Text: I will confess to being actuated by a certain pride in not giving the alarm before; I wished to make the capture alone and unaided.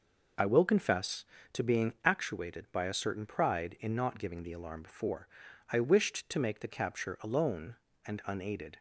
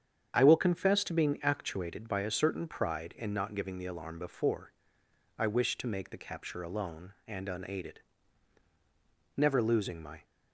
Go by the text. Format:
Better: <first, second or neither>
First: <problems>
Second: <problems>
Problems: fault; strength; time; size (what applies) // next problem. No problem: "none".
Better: first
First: none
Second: starts louder than the rest; strong; until 1.3 s; 8 dB // goes on to say "Never losing my"; noticeable; from 9.3 s on; 0.86 s long